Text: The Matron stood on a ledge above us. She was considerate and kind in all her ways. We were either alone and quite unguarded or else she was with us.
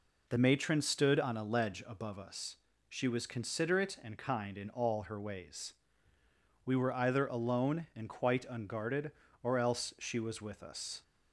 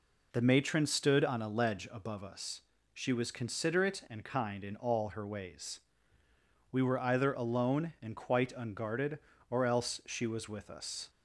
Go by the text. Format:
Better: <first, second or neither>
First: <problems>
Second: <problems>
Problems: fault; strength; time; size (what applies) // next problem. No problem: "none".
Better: neither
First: none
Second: none